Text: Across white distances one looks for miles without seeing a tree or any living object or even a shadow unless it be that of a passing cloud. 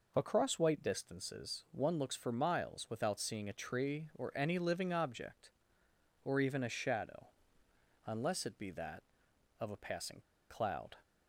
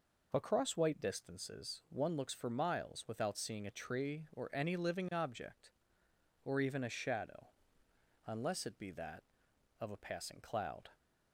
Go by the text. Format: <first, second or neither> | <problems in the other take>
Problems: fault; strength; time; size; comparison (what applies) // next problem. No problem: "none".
second | pauses between "shadow" and "unless"; noticeable; at 7.2 s; 0.76 s long; noticeable in the second // pauses between "passing" and "cloud"; slight; at 10.2 s; 0.29 s long